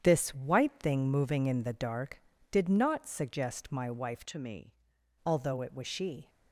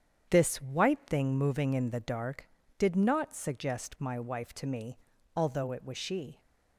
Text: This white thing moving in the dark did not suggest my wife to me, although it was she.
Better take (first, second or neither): second